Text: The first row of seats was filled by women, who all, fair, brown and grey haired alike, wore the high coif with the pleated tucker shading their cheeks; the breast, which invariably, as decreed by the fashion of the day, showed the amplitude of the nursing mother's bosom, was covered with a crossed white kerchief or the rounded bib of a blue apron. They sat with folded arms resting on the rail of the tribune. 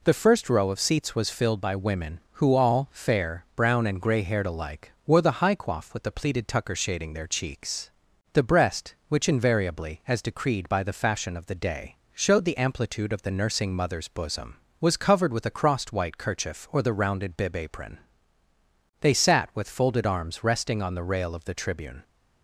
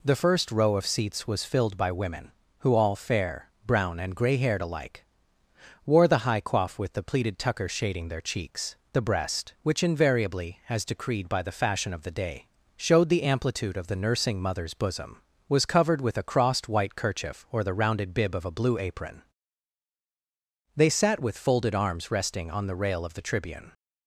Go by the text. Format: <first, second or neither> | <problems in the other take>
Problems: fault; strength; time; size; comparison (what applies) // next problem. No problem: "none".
second | skips "of a blue"; at 17.5 s